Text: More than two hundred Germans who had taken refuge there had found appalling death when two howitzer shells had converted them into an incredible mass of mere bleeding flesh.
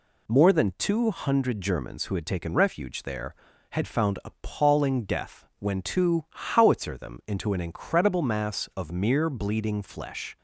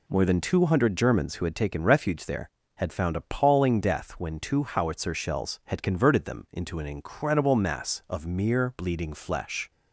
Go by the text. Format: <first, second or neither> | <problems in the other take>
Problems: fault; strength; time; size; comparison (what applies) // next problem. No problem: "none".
second | skips "shells had converted"; at 6.9 s